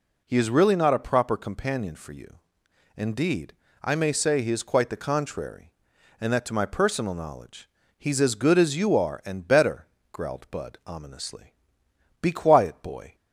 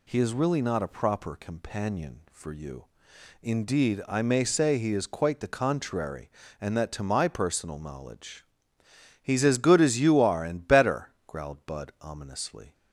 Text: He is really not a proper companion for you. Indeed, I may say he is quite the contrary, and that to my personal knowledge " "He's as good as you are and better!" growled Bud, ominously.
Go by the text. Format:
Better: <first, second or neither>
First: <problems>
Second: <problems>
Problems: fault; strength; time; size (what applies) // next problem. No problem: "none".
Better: second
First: goes on to say "Be quiet boy"; noticeable; from 12.2 s on; 0.94 s long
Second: none